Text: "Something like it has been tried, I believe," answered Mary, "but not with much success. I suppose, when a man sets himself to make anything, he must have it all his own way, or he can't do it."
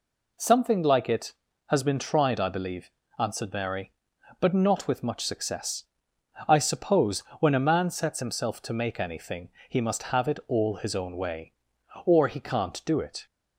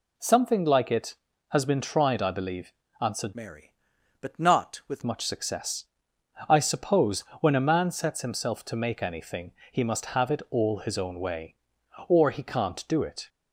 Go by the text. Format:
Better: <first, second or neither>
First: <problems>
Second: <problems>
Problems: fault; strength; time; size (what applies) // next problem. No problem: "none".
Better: first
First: none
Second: changes voice from "Mary" to "with"; from 3.3 to 5.0 s; 1.7 s long